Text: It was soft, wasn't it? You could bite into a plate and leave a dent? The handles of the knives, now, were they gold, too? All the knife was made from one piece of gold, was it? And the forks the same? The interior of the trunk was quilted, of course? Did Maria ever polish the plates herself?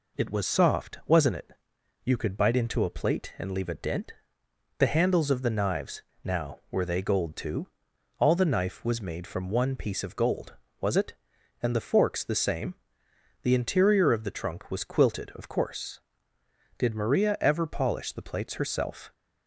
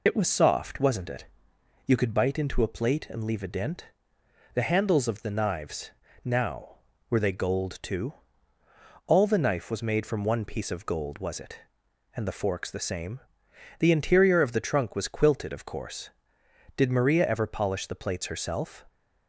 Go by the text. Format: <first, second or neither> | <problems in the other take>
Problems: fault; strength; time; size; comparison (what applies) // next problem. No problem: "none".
first | loses the start of "It"; at 0.0 s; 55 ms